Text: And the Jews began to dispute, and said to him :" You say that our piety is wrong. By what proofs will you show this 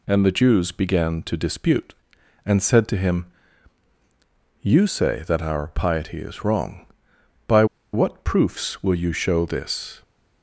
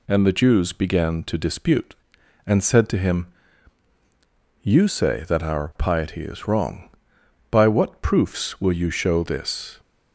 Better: second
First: pauses between "By" and "what"; slight; at 7.6 s; 0.28 s long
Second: none

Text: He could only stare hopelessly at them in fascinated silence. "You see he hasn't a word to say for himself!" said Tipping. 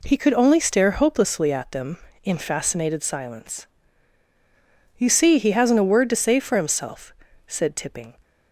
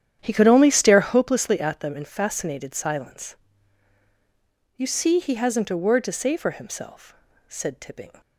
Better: first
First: none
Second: starts louder than the rest; strong; until 1.4 s; 9.5 dB

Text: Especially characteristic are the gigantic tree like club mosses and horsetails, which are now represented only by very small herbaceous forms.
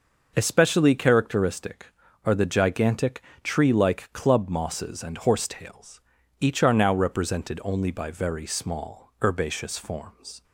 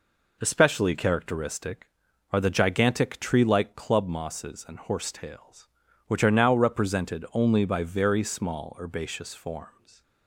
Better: second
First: pauses between "gigantic" and "tree"; slight; at 3.2 s; 0.22 s long // says "each" for "which"; at 6.4 s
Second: none

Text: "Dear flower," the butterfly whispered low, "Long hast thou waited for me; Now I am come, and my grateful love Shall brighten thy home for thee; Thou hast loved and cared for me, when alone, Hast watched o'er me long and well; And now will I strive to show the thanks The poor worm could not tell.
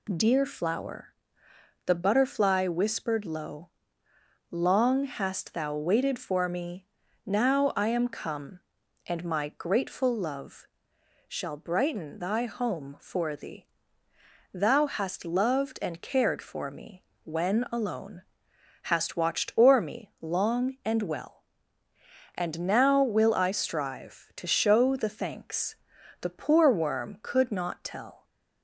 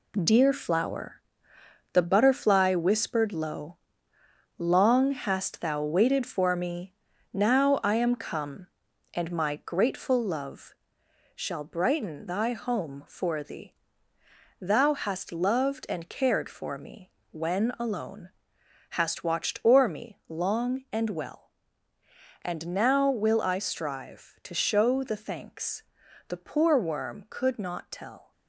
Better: first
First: pauses between "love" and "Shall"; noticeable; at 10.6 s; 0.62 s long // pauses between "thanks" and "The"; noticeable; at 25.7 s; 0.46 s long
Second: gets quieter; throughout; 7 dB // pauses between "love" and "Shall"; noticeable; at 10.7 s; 0.62 s long // pauses between "thanks" and "The"; noticeable; at 25.8 s; 0.46 s long

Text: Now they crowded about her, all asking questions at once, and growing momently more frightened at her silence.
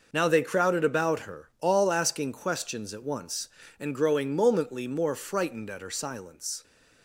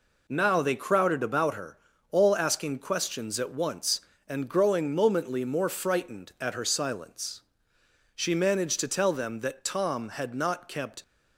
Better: first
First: none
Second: goes on to say "She managed to tell them that Tom had not kept"; strong; from 8.1 s on; 2.8 s long

